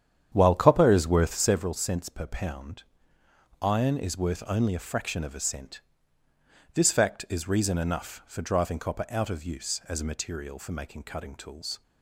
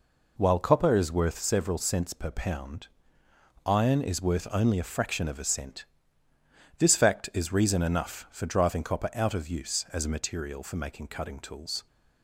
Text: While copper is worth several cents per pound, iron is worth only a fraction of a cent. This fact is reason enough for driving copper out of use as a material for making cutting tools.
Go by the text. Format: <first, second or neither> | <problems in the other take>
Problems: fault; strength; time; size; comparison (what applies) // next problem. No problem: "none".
second | starts louder than the rest; strong; until 1.6 s; 9 dB